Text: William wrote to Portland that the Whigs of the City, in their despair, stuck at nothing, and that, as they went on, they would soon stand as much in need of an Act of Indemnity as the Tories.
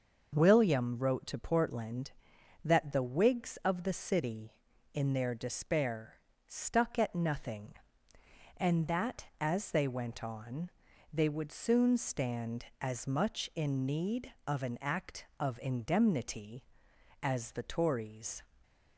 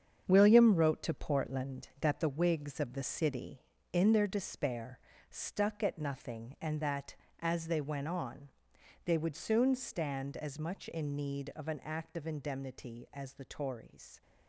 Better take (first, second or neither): first